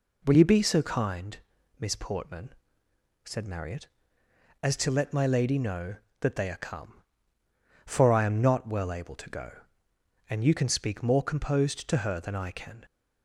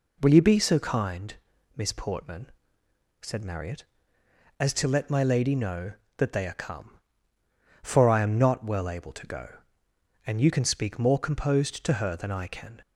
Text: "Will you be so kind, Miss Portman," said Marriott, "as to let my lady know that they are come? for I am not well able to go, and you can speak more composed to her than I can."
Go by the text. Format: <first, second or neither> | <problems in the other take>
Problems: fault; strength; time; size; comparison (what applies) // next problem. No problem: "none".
neither | none